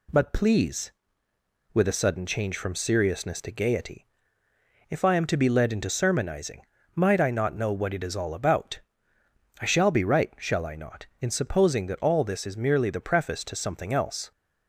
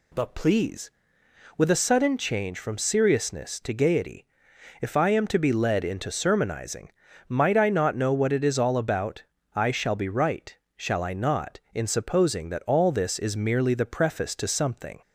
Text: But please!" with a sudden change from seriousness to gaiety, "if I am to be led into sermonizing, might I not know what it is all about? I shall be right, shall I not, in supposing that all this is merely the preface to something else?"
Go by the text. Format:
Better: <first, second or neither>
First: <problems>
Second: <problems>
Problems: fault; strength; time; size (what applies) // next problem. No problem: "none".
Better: first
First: none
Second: stops before "else"; at 15.0 s